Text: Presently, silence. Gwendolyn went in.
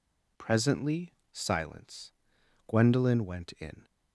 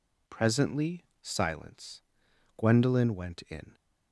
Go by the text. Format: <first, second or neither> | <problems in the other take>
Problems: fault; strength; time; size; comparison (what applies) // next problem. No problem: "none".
neither | none